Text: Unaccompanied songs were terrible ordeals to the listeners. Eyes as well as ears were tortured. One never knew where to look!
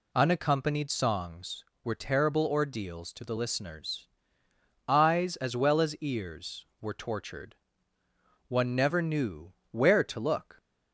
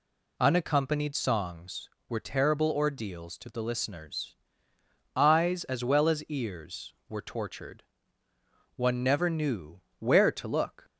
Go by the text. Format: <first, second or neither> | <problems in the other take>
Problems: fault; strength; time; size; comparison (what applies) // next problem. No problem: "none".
neither | pauses between "knew" and "where"; slight; the same in both